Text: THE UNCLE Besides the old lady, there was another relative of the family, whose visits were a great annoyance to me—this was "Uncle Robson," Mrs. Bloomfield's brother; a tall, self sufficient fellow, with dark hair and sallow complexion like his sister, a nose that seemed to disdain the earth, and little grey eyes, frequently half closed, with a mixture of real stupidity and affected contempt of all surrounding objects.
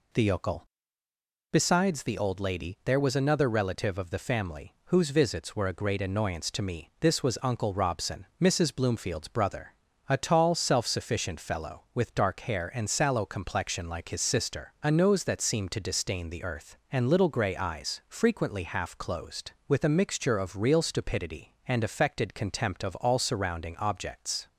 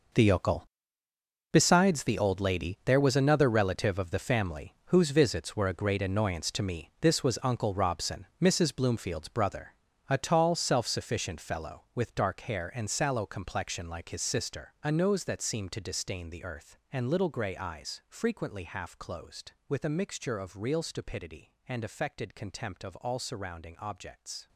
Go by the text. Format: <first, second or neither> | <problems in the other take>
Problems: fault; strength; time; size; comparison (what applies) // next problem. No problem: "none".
first | gets quieter; strong; throughout; 14 dB // pauses between "UNCLE" and "Besides"; noticeable; at 0.6 s; 0.86 s long; noticeable in the first